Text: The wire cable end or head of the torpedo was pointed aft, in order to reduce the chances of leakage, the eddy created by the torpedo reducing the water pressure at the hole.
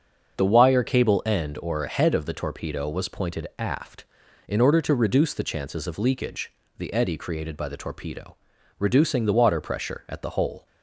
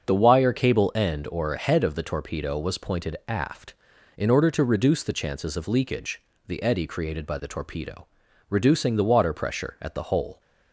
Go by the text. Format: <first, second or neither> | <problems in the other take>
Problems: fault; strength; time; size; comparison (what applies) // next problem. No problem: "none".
neither | starts louder than the rest; the same in both // pauses between "torpedo" and "reducing"; the same in both